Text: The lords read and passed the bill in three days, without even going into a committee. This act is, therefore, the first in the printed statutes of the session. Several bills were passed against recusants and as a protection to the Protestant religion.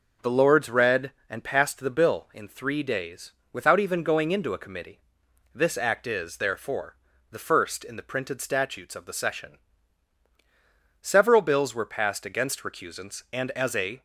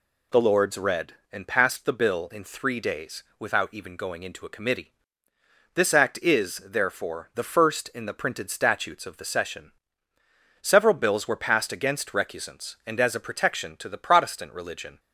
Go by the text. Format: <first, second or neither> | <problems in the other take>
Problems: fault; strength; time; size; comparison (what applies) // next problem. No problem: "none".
second | stops before "protection to the Protestant religion"; at 13.9 s